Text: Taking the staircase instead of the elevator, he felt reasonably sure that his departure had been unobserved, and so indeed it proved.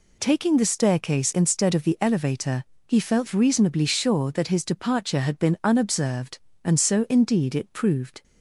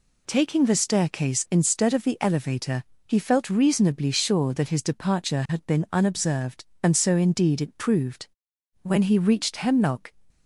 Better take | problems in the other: first | goes on to say "When he reached Hemlock"; noticeable; from 8.8 s on; 1.3 s long

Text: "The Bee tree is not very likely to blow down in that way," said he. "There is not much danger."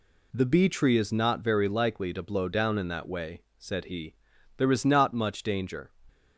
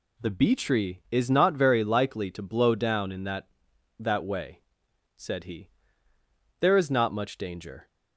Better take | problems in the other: first | says "that" twice; at 3.9 s

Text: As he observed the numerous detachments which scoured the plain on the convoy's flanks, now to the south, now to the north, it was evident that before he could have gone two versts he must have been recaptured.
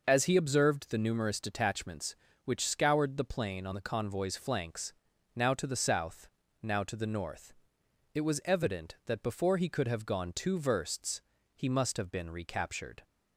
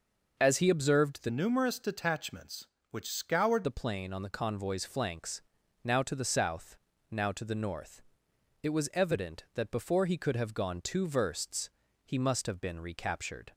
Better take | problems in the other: first | changes voice from "numerous" to "scoured"; from 1.2 to 3.6 s; 2.4 s long // pauses between "versts" and "he"; slight; at 11.6 s; 0.34 s long; slight in the first

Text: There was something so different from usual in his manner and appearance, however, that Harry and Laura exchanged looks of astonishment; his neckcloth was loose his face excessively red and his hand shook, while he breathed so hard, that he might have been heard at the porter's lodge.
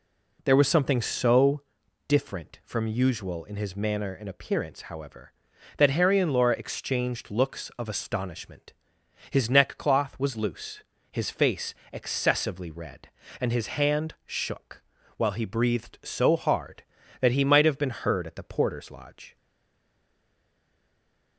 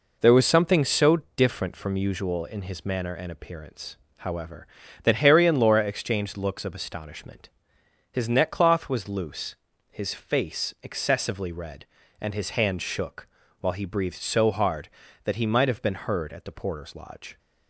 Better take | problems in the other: second | pauses between "so" and "different"; noticeable; at 1.6 s; 0.48 s long; slight in the second // pauses between "loose" and "his"; slight; at 10.8 s; 0.28 s long; also in the second // pauses between "face" and "excessively"; slight; at 11.7 s; 0.18 s long // stays silent after the last word; noticeable; from 19.3 s on; 2.0 s long

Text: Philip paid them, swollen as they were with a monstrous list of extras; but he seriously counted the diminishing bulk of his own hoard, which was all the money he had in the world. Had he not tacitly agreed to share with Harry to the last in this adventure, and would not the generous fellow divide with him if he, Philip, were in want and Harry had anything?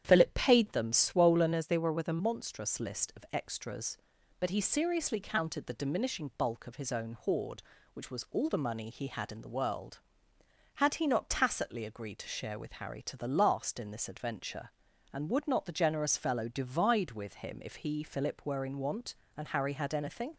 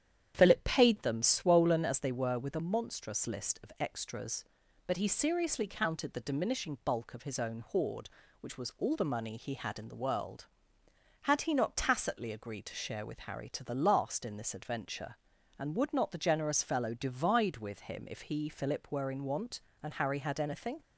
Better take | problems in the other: second | starts louder than the rest; strong; until 1.0 s; 9.5 dB; strong in the second // changes voice from "as" to "a"; from 1.5 to 2.2 s; 0.7 s long

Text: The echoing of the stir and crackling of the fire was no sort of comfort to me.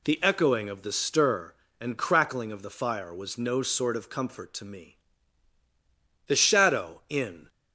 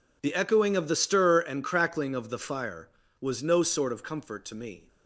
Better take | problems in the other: second | goes on to say "The shadow in"; noticeable; from 6.2 s on; 1.2 s long

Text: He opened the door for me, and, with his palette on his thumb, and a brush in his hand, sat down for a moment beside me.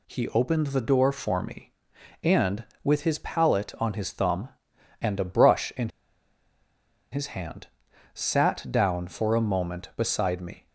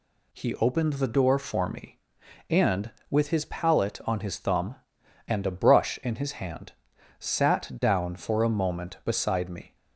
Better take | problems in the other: second | pauses between "in" and "his"; at 5.8 s; 1.2 s long

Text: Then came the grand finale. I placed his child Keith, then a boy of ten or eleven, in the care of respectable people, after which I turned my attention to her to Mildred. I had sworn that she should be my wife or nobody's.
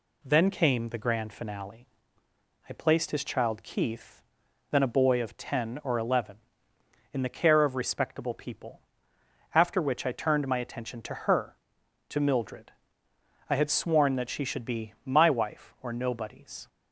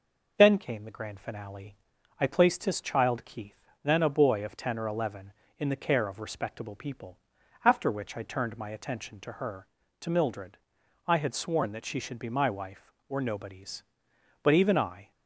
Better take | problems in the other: first | goes on to say "But even I"; noticeable; from 14.4 s on; 0.68 s long

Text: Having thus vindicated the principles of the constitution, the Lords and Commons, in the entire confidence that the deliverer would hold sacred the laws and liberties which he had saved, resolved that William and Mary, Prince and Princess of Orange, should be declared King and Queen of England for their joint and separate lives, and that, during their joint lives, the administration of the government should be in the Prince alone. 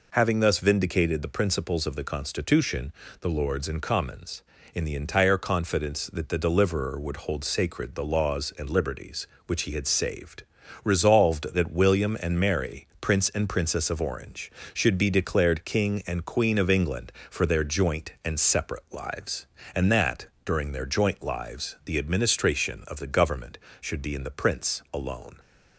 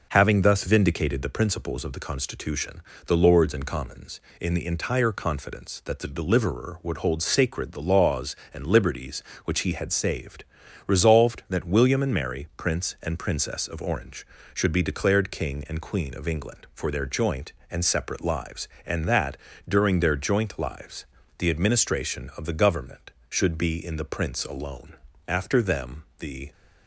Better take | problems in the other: first | goes on to say "After them the"; noticeable; from 25.2 s on; 1.2 s long

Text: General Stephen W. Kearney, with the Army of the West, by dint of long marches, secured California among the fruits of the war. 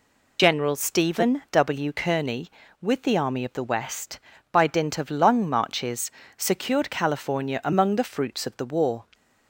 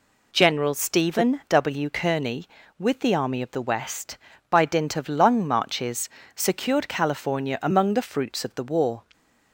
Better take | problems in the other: second | loses the start of "General"; at 0.3 s; 45 ms

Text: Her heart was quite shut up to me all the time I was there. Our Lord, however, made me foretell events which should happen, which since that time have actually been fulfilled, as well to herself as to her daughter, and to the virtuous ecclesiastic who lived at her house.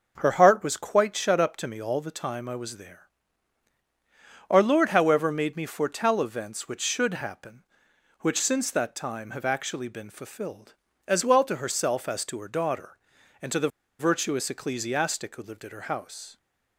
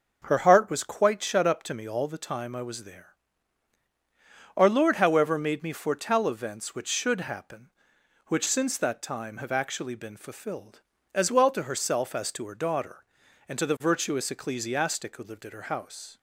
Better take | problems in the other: second | starts louder than the rest; until 1.2 s; 7 dB; also in the second // pauses between "the" and "virtuous"; slight; at 13.6 s; 0.30 s long

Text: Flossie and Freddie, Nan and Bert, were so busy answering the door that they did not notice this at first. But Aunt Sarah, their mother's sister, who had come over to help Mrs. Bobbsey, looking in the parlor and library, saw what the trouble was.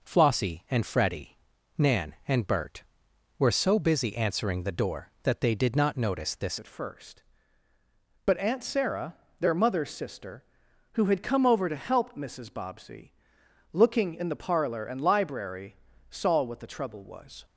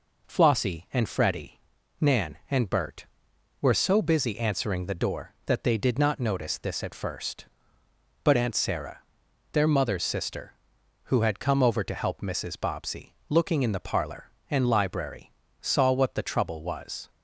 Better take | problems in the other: second | changes voice at "at"; from 6.5 s on; 10.9 s long

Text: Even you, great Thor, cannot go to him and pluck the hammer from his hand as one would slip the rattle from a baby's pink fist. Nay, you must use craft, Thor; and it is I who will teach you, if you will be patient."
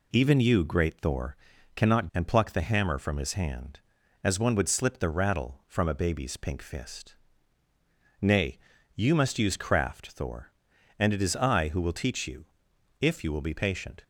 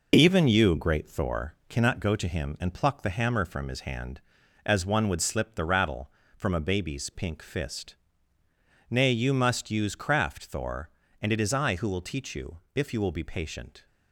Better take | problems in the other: second | skips "go to him"; at 2.1 s

